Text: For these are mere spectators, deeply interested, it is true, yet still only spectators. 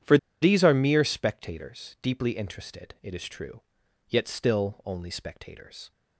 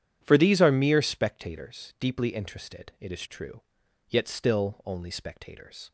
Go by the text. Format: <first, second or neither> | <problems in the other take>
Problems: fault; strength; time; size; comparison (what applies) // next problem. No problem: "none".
second | pauses between "For" and "these"; slight; at 0.1 s; 0.25 s long